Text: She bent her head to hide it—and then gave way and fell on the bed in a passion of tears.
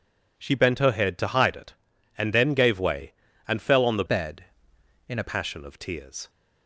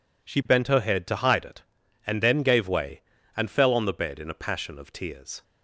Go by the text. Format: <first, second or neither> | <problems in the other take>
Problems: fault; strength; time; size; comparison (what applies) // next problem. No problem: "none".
second | changes voice from "bed" to "a"; from 4.0 to 5.2 s; 1.2 s long